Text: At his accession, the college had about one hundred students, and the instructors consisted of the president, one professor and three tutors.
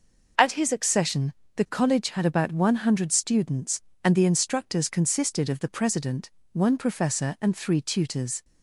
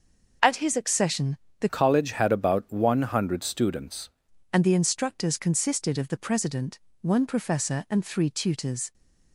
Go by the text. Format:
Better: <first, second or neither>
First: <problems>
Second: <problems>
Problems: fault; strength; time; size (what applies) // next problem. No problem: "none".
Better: first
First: none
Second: changes voice from "college" to "students"; from 1.6 to 4.1 s; 2.5 s long